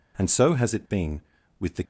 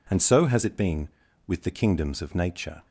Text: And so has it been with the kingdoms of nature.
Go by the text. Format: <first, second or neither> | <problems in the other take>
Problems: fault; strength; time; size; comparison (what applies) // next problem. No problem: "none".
second | stops before "kingdoms of nature"; at 1.8 s